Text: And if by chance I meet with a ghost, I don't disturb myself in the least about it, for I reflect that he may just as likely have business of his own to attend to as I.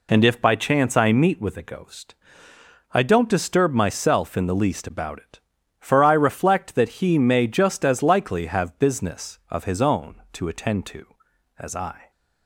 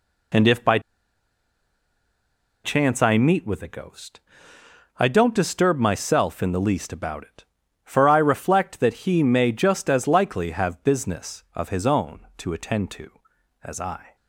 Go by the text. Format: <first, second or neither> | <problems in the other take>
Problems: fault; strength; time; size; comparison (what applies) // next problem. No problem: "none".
first | pauses between "by" and "chance"; strong; at 0.7 s; 1.8 s long